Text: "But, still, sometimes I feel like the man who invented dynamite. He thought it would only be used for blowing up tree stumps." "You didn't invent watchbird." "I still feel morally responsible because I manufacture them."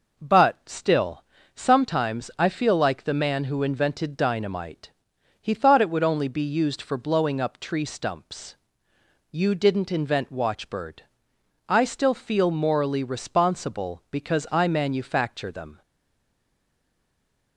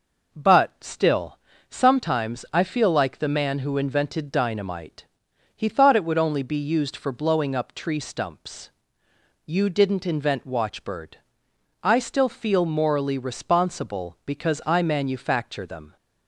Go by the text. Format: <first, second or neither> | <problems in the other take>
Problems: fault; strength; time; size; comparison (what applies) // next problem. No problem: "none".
second | stays silent after the last word; noticeable; from 15.8 s on; 1.7 s long